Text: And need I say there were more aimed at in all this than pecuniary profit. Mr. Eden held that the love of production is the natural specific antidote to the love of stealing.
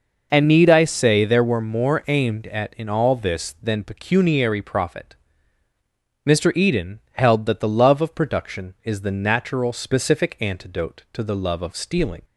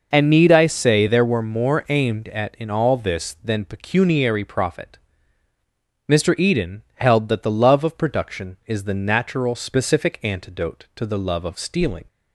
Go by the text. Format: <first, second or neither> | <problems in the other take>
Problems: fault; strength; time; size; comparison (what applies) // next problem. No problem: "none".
neither | none